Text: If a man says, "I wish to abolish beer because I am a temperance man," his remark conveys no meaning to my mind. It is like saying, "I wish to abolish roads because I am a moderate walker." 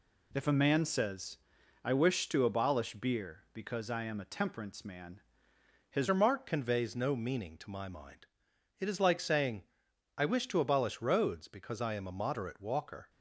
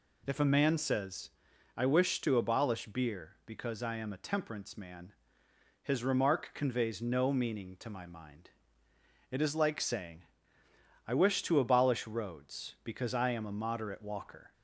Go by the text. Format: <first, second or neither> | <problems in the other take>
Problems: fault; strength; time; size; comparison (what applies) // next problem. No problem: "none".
second | changes voice at "remark"; from 6.0 s on; 7.0 s long